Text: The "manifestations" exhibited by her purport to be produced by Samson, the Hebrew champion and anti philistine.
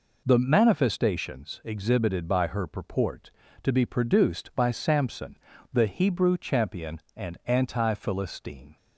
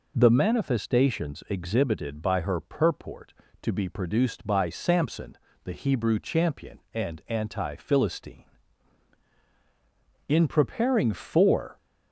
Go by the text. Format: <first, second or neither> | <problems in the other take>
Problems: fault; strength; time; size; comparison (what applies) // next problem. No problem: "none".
first | goes on to say "In preparing for"; from 10.2 s on; 1.4 s long